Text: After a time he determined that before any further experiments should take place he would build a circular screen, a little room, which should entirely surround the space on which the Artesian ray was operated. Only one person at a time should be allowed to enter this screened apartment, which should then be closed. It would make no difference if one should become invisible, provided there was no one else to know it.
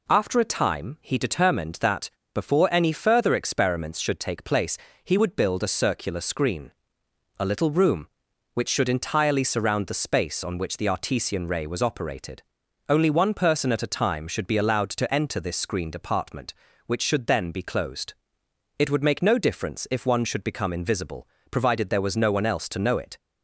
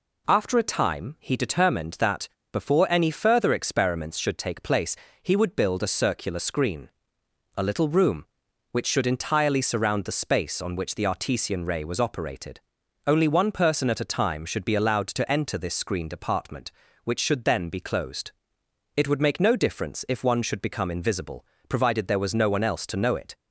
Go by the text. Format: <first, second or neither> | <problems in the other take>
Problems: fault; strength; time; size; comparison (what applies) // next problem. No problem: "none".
neither | pauses between "that" and "before"; slight; the same in both // pauses between "place" and "he"; slight; the same in both